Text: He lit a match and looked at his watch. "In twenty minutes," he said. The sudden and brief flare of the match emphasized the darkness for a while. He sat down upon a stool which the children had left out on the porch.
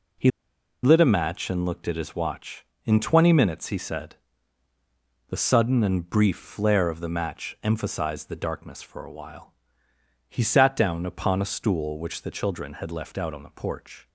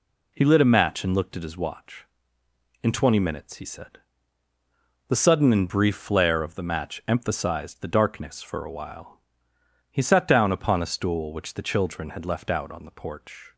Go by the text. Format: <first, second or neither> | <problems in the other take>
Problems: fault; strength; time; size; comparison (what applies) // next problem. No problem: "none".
second | pauses between "He" and "lit"; noticeable; at 0.3 s; 0.53 s long